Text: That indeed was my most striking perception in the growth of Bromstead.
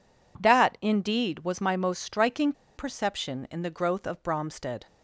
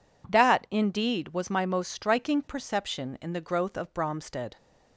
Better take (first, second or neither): second